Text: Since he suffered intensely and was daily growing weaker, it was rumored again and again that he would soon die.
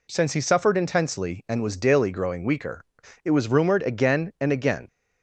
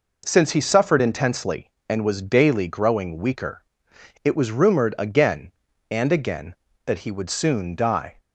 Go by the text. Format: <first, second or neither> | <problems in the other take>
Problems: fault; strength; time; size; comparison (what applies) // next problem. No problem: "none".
second | stops before "that he would soon die"; at 4.8 s